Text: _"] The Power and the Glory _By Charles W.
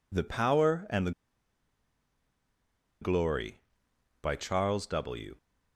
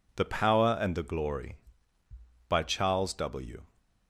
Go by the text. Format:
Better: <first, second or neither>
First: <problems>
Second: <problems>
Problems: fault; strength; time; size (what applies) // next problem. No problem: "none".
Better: second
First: pauses between "the" and "Glory"; strong; at 1.1 s; 1.9 s long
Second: none